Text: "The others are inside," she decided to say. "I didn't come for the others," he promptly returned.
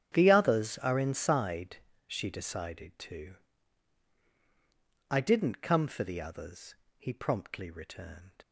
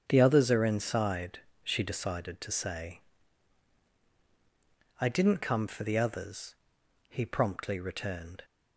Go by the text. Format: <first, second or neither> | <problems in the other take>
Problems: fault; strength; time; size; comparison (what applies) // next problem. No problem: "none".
second | starts louder than the rest; strong; until 1.1 s; 9 dB; strong in the second // skips "say"; at 4.2 s